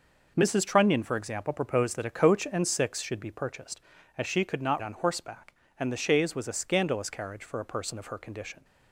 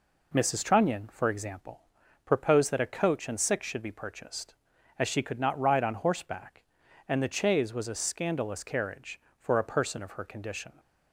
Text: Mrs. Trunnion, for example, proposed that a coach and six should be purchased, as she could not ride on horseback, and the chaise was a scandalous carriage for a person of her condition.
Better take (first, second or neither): second